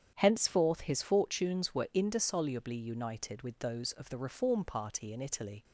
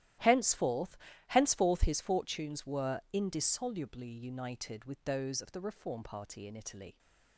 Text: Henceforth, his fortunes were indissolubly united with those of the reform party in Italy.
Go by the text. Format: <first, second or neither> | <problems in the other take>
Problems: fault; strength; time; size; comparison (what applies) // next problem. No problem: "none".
first | starts louder than the rest; strong; until 1.5 s; 13.5 dB; strong in the first // says "Henceforth" twice; at 1.2 s